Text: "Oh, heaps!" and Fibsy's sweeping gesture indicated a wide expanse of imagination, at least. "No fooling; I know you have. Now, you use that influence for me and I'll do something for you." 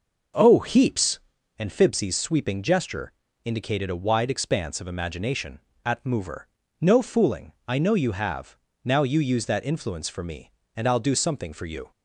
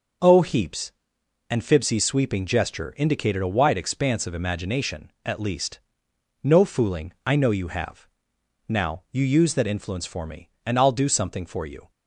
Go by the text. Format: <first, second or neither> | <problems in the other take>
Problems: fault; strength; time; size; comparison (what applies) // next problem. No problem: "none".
second | pauses between "gesture" and "indicated"; slight; at 3.1 s; 0.32 s long // says "mover" for "least"; at 6.0 s